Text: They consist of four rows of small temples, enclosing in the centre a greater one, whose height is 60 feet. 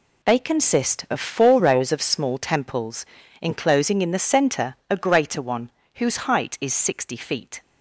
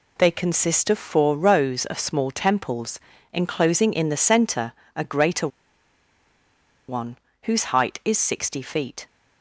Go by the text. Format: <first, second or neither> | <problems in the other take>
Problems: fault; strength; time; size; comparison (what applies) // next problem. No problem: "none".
first | pauses between "centre" and "a"; slight; at 4.7 s; 0.22 s long // pauses between "greater" and "one"; strong; at 5.4 s; 1.4 s long